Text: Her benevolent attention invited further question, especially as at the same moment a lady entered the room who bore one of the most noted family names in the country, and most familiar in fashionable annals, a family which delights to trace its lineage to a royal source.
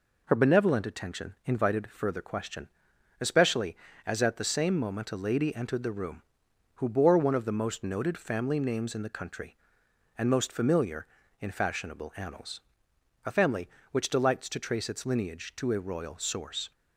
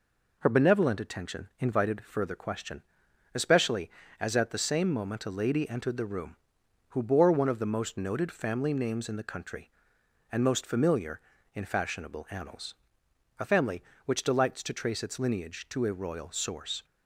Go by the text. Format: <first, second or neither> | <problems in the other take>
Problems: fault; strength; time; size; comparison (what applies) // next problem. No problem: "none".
neither | none